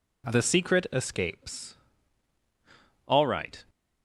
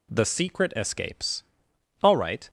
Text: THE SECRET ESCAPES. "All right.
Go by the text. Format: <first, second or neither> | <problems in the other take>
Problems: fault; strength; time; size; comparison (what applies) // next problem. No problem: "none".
neither | none